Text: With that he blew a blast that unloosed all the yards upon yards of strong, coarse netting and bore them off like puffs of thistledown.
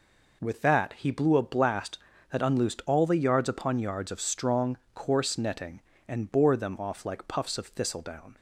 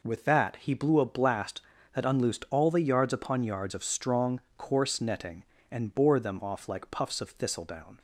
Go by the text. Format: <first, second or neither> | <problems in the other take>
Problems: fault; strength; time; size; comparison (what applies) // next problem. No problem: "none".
neither | none